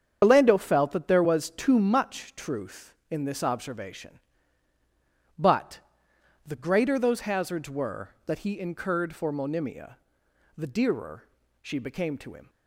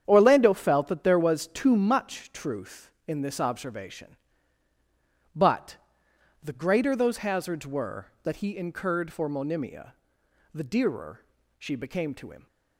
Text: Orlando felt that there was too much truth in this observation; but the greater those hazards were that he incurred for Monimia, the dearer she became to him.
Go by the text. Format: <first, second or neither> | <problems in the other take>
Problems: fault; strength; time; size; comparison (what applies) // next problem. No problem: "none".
second | loses the start of "Orlando"; at 0.2 s; 115 ms // starts louder than the rest; strong; until 1.2 s; 8 dB; strong in the second // pauses between "but" and "the"; noticeable; at 5.7 s; 0.66 s long; noticeable in the second // pauses between "dearer" and "she"; at 11.2 s; 0.38 s long; also in the second